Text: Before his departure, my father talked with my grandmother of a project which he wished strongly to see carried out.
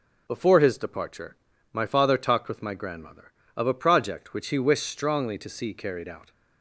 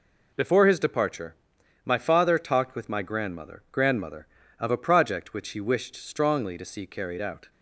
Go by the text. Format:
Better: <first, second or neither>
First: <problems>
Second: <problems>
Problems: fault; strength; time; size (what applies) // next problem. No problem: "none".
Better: first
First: none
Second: says "grandmother" twice; at 3.7 s